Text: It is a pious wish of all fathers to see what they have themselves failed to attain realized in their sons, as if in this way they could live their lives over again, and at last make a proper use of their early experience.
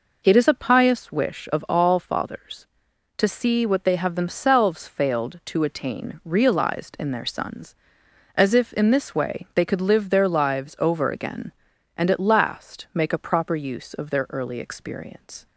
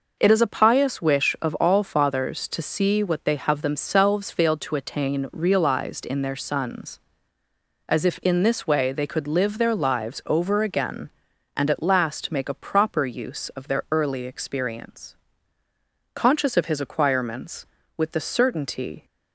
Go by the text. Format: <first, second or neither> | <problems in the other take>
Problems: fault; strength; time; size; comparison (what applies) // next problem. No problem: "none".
first | goes on to say "Conscious of his acquirements with the certainty"; strong; from 16.1 s on; 2.9 s long